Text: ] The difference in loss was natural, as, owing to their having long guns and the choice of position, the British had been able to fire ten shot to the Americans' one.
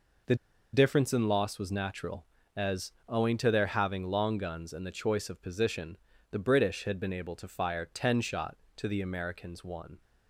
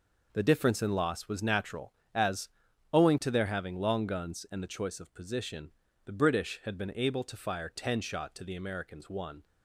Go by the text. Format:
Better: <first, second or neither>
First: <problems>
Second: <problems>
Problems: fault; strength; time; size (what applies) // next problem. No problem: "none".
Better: second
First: pauses between "The" and "difference"; at 0.3 s; 0.38 s long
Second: none